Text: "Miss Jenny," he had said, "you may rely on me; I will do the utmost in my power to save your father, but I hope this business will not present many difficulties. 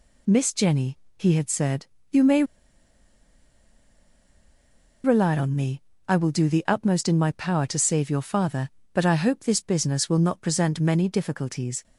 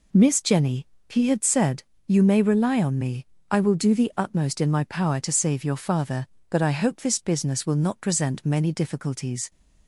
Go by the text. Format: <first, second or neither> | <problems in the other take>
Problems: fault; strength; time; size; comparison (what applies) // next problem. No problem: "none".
second | pauses between "may" and "rely"; strong; at 2.4 s; 2.6 s long